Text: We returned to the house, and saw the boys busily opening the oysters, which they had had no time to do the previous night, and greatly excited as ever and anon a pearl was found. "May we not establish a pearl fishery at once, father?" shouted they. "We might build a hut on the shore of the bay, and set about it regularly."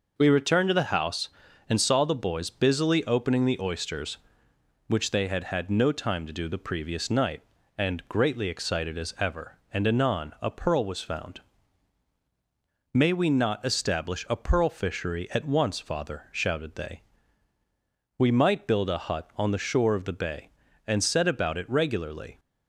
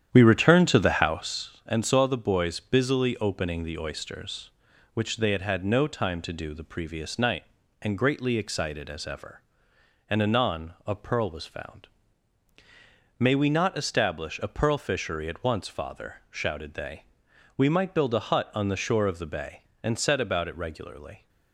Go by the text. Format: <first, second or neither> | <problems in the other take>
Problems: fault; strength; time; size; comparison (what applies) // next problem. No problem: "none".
first | starts louder than the rest; strong; until 1.4 s; 10 dB